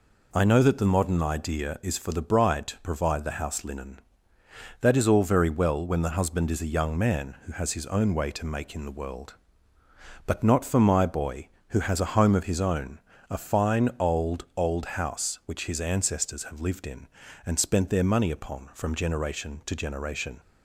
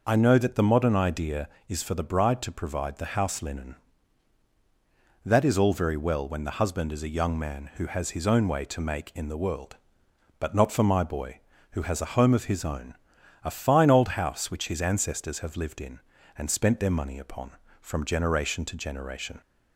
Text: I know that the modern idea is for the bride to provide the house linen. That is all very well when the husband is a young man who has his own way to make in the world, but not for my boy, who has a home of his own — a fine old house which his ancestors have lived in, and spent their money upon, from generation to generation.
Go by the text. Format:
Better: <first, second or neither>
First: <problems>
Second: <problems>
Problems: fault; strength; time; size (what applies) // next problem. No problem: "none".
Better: second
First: says "old" twice; at 14.5 s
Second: none